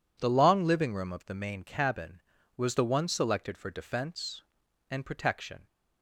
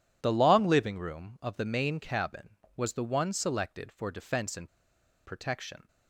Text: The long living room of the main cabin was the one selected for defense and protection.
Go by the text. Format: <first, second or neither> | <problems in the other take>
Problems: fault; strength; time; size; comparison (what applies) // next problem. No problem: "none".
first | pauses between "and" and "protection"; noticeable; at 4.6 s; 0.58 s long